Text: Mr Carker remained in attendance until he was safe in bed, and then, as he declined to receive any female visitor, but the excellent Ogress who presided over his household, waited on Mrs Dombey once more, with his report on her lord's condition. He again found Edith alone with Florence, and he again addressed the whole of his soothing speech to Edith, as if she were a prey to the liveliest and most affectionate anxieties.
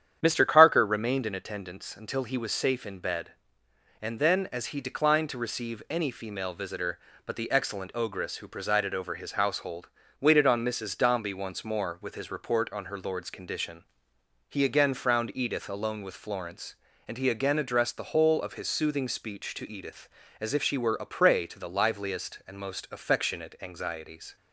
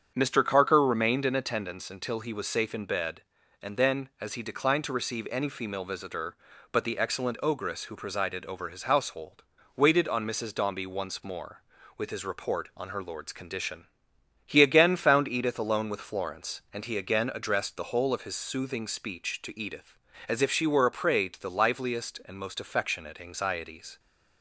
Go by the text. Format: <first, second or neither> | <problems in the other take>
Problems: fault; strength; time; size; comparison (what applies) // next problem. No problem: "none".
second | starts louder than the rest; strong; until 1.2 s; 9.5 dB; strong in the second // says "frowned" for "found"; at 14.9 s